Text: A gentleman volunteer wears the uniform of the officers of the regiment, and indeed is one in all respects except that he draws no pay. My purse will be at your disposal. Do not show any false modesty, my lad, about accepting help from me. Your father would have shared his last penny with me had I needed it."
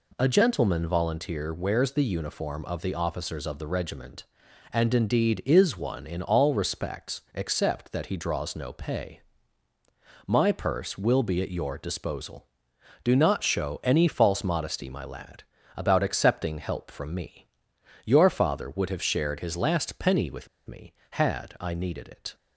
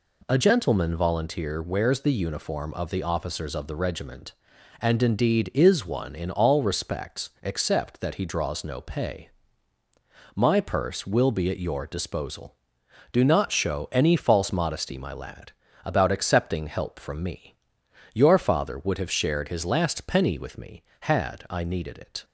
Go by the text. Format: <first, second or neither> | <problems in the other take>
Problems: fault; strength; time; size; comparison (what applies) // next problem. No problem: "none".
second | pauses between "with" and "me"; slight; at 20.4 s; 0.21 s long